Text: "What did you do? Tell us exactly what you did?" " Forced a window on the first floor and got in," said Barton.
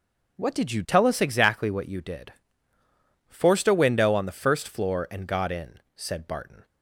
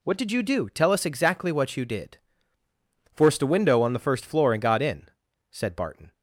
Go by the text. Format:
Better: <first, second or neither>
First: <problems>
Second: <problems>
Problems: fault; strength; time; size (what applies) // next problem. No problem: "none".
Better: second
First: skips "do"; at 0.8 s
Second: none